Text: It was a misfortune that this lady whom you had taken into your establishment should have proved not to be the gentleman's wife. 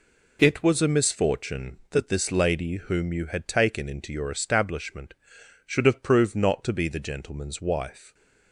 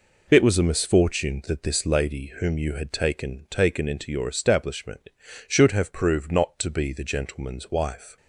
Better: first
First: none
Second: says "taken" twice; at 3.4 s

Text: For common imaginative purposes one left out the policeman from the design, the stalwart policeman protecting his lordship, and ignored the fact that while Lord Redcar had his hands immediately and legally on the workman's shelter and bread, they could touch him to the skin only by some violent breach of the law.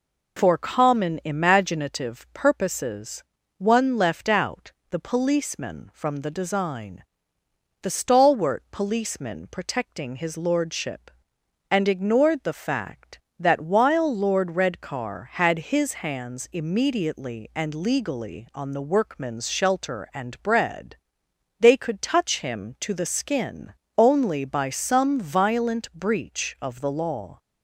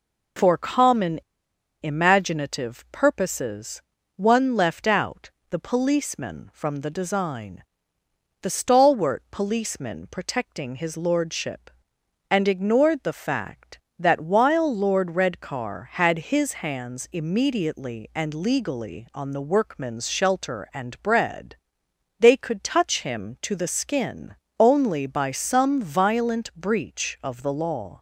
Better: first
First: pauses between "purposes" and "one"; slight; at 3.2 s; 0.34 s long // pauses between "out" and "the"; slight; at 4.7 s; 0.18 s long // pauses between "skin" and "only"; slight; at 23.7 s; 0.24 s long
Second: pauses between "common" and "imaginative"; noticeable; at 1.1 s; 0.62 s long // pauses between "purposes" and "one"; slight; at 3.8 s; 0.34 s long // pauses between "out" and "the"; slight; at 5.2 s; 0.20 s long // pauses between "skin" and "only"; slight; at 24.3 s; 0.24 s long

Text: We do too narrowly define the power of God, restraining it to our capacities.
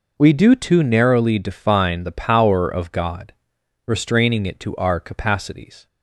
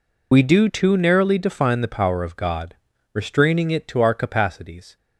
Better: first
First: none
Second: loses the start of "We"; at 0.3 s; 25 ms

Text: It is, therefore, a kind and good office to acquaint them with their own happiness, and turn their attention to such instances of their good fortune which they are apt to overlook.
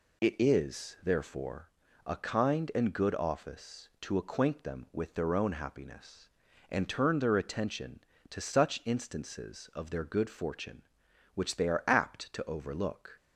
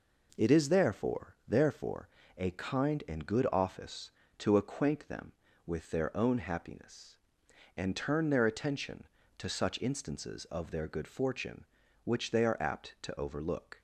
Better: first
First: none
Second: says "therefore" twice; at 1.4 s

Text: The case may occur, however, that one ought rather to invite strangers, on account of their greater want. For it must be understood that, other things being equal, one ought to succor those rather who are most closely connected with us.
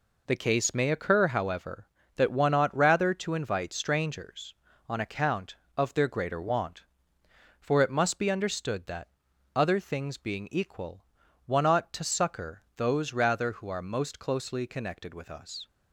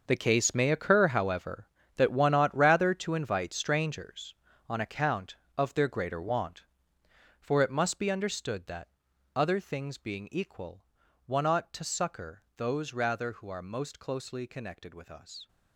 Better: first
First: pauses between "succor" and "those"; slight; at 12.6 s; 0.16 s long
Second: gets quieter; strong; throughout; 13 dB // pauses between "succor" and "those"; slight; at 12.4 s; 0.16 s long

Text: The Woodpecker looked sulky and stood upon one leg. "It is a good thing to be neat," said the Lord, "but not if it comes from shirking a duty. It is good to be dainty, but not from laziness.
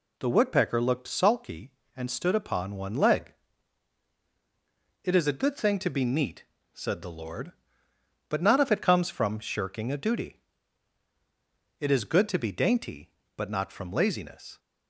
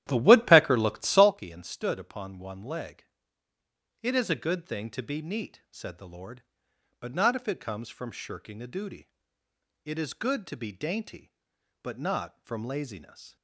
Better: first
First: none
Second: starts louder than the rest; strong; until 1.4 s; 12.5 dB

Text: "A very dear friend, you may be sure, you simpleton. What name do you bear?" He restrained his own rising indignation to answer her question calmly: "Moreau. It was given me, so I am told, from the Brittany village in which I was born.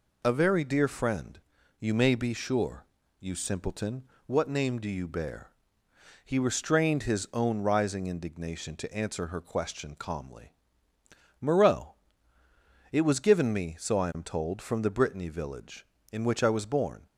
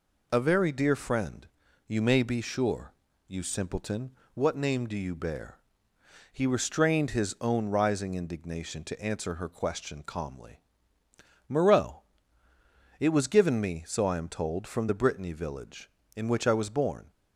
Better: neither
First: none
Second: none

